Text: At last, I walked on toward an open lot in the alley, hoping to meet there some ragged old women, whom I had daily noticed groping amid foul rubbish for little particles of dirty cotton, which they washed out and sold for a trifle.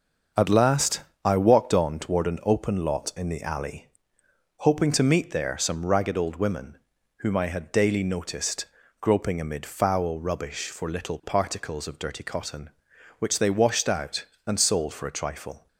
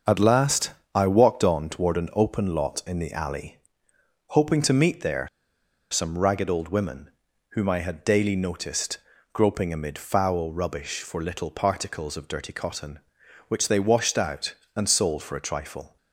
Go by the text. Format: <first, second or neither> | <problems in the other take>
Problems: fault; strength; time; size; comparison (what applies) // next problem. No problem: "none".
first | starts louder than the rest; until 1.2 s; 6 dB; also in the first // pauses between "there" and "some"; noticeable; at 5.2 s; 0.62 s long // pauses between "noticed" and "groping"; slight; at 8.9 s; 0.34 s long; slight in the first